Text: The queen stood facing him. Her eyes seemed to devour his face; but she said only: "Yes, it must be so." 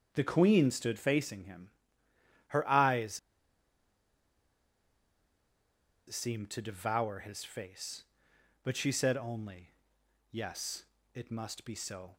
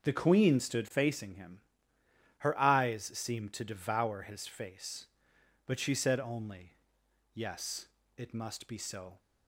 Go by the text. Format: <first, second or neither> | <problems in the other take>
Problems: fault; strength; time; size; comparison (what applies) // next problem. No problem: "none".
second | starts louder than the rest; until 1.1 s; 6.5 dB; also in the second // pauses between "eyes" and "seemed"; strong; at 3.1 s; 2.9 s long